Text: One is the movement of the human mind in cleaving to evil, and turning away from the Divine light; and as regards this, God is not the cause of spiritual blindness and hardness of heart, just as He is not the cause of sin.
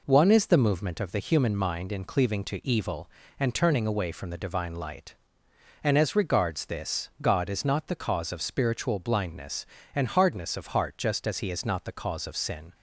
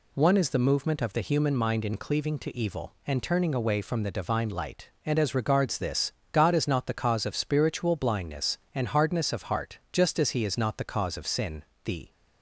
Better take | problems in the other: first | goes on to say "The"; slight; from 11.8 s on; 0.26 s long

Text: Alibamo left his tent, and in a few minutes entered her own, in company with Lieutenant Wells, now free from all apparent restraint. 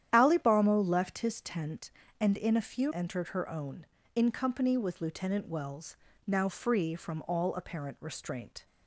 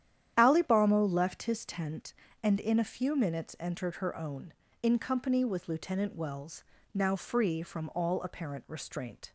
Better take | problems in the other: second | starts louder than the rest; strong; until 1.1 s; 10.5 dB; strong in the second // skips "minutes"; at 2.9 s

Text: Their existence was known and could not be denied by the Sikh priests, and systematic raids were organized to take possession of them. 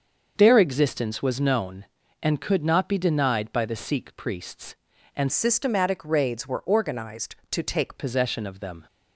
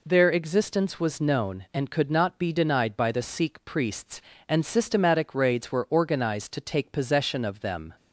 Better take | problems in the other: second | starts louder than the rest; until 1.3 s; 6.5 dB // changes voice from "systematic" to "take"; from 5.3 to 7.9 s; 2.6 s long

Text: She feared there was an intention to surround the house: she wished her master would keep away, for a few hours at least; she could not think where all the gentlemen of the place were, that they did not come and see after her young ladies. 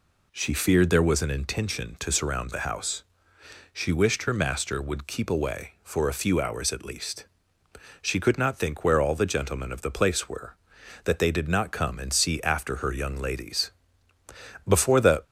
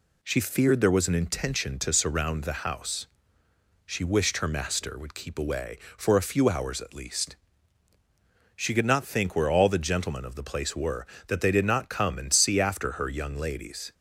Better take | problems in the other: second | goes on to say "Before the"; from 14.6 s on; 0.56 s long

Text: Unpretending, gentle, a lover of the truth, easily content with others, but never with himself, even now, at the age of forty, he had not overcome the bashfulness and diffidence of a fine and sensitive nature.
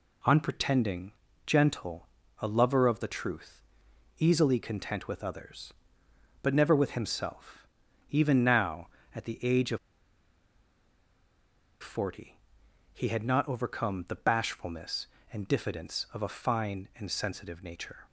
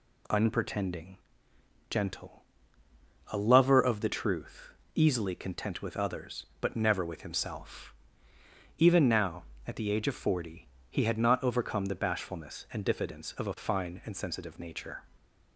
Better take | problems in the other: second | pauses between "of" and "forty"; strong; at 9.7 s; 2.0 s long

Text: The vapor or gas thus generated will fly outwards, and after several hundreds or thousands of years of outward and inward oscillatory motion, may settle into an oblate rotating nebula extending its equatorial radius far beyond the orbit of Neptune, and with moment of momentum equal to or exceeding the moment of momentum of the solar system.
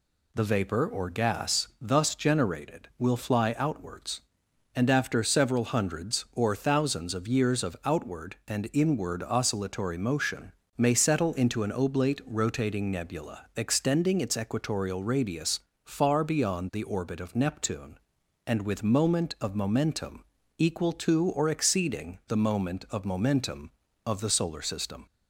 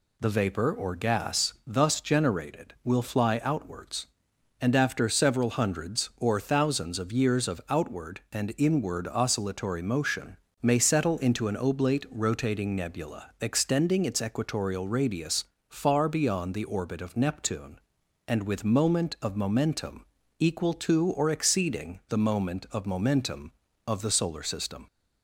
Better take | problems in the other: neither | pauses between "radius" and "far"; slight; the same in both // pauses between "momentum" and "equal"; slight; the same in both

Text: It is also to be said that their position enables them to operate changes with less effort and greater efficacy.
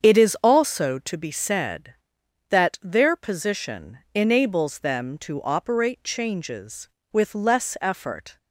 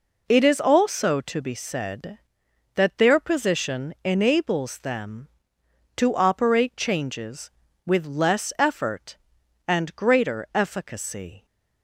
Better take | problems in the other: second | starts louder than the rest; strong; until 1.0 s; 7.5 dB // pauses between "position" and "enables"; slight; at 3.9 s; 0.16 s long // stops before "and greater efficacy"; at 8.3 s

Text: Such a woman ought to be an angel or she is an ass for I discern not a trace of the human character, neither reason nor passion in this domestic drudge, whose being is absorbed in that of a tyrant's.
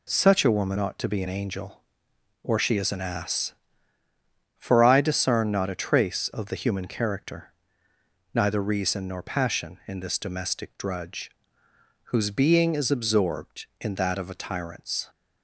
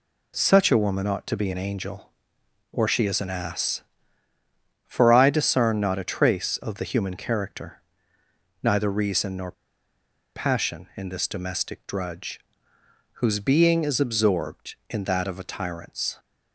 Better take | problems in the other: first | pauses between "nor" and "passion"; noticeable; at 9.5 s; 0.82 s long

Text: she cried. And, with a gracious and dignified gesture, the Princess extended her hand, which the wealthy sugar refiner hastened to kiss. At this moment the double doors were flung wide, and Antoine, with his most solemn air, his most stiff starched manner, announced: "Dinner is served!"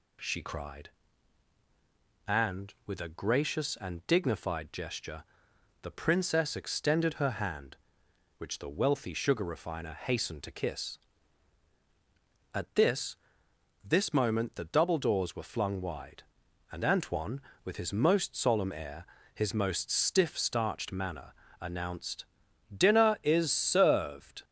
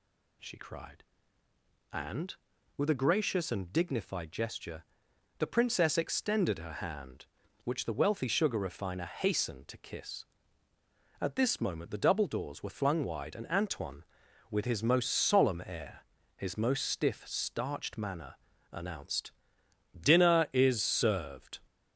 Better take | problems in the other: second | says "this" twice; at 13.8 s

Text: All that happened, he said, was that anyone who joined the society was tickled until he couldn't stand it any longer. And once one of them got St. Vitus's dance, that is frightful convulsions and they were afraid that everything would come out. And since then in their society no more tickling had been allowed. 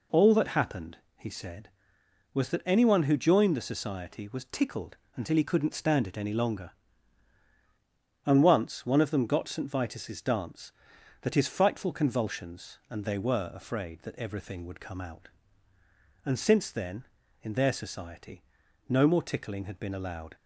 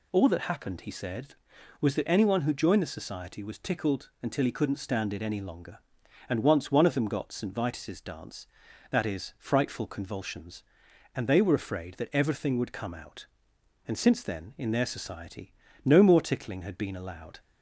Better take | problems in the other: second | pauses between "tickled" and "until"; slight; at 4.9 s; 0.18 s long // says "his" for "is"; at 11.3 s // pauses between "society" and "no"; at 18.4 s; 0.44 s long; slight in the second

